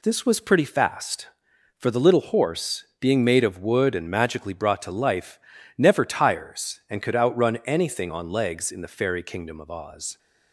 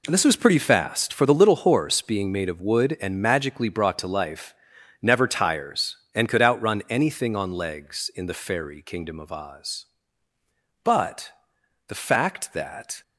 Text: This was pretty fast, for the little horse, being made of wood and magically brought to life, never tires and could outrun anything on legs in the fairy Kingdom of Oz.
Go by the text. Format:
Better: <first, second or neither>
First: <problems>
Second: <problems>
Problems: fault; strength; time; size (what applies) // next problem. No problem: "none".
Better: first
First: none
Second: goes on to say "But the fact that"; strong; from 10.8 s on; 2.1 s long